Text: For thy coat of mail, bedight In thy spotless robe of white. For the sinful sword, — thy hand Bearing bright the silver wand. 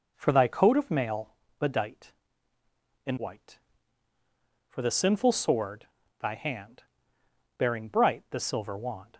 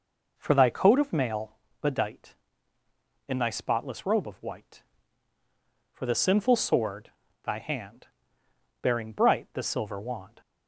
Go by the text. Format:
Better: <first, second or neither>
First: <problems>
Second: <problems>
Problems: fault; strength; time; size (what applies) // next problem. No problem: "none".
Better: second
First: skips "thy spotless robe of"; at 3.1 s // pauses between "hand" and "Bearing"; noticeable; at 6.8 s; 0.74 s long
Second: pauses between "hand" and "Bearing"; noticeable; at 8.0 s; 0.74 s long